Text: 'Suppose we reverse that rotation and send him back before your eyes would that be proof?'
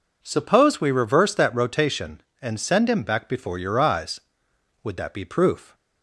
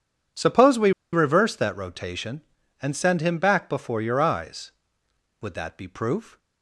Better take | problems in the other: first | pauses between "we" and "reverse"; slight; at 0.9 s; 0.22 s long

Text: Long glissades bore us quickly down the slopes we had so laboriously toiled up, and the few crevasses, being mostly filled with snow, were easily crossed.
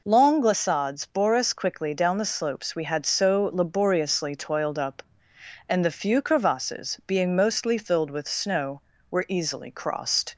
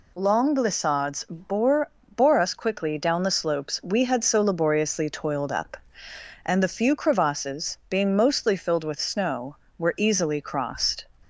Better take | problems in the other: first | says "bore" twice; at 2.1 s

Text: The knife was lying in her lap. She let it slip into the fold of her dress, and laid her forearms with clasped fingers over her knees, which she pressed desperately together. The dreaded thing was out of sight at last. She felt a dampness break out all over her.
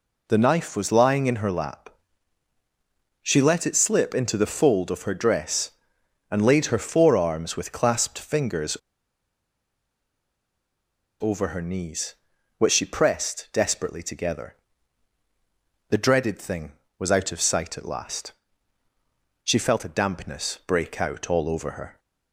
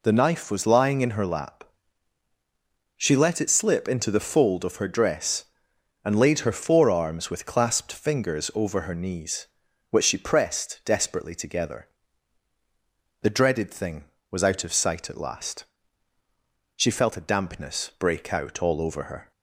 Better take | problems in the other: second | pauses between "fingers" and "over"; strong; at 8.7 s; 2.4 s long

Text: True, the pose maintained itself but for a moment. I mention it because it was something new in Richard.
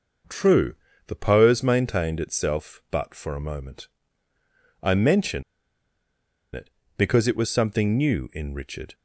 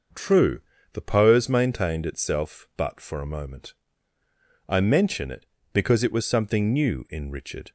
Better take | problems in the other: second | pauses between "mention" and "it"; at 5.4 s; 1.1 s long

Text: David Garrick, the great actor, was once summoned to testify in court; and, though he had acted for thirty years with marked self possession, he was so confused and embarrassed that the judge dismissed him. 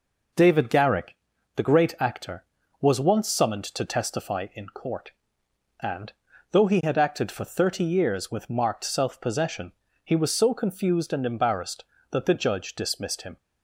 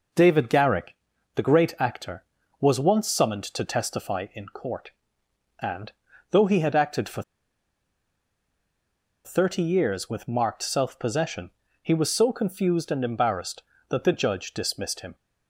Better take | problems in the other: first | pauses between "for" and "thirty"; strong; at 7.2 s; 2.0 s long

